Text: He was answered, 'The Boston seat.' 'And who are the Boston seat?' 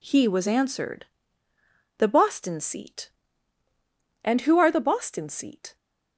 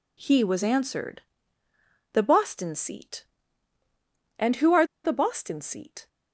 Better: first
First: none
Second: pauses between "are" and "the"; slight; at 4.8 s; 0.19 s long

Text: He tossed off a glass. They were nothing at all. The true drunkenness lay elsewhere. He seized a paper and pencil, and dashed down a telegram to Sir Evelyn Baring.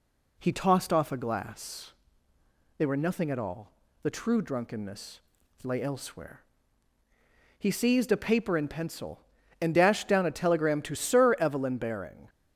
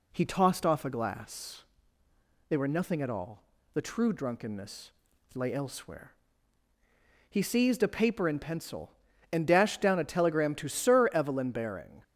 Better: neither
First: pauses between "drunkenness" and "lay"; noticeable; at 5.1 s; 0.46 s long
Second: pauses between "drunkenness" and "lay"; noticeable; at 4.8 s; 0.46 s long

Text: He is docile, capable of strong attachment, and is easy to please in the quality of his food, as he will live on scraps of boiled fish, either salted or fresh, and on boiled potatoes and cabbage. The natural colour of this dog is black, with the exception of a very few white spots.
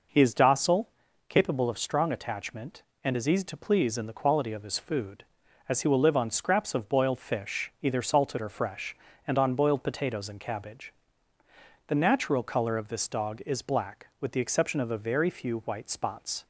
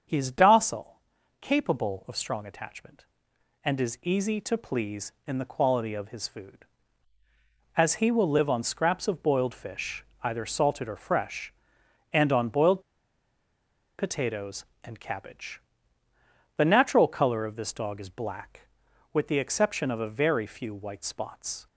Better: first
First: none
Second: starts louder than the rest; until 1.4 s; 7 dB // pauses between "boiled" and "potatoes"; at 12.8 s; 1.1 s long

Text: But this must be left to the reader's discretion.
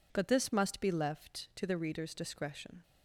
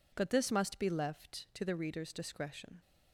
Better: neither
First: none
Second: none

